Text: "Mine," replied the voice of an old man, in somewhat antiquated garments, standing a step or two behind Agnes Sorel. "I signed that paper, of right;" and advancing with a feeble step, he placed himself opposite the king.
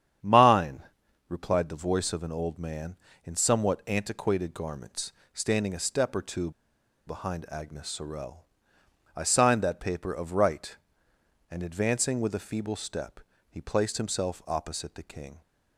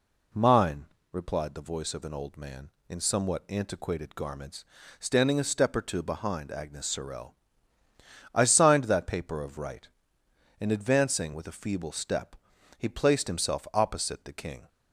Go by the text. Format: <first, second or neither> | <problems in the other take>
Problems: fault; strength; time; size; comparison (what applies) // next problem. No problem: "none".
second | starts louder than the rest; strong; until 1.6 s; 9 dB // pauses between "two" and "behind"; noticeable; at 6.5 s; 0.56 s long